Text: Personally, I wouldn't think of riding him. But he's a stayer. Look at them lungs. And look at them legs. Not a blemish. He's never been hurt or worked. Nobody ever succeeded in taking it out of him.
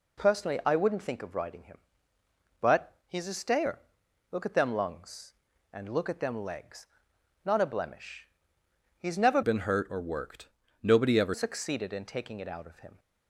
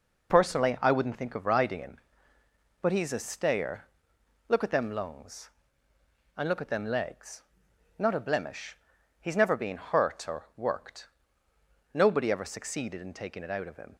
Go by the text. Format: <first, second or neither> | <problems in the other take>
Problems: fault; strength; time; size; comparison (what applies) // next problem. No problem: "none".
second | changes voice from "been" to "ever"; from 9.4 to 11.3 s; 1.9 s long